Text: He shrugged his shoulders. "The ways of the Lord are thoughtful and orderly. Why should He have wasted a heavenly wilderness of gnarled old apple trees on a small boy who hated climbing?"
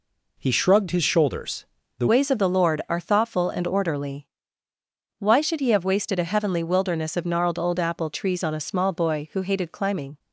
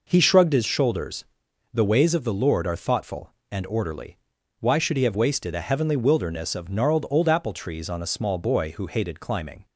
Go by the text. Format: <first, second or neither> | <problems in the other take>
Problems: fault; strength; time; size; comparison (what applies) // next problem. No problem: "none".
second | changes voice at "ways"; from 2.0 s on; 8.1 s long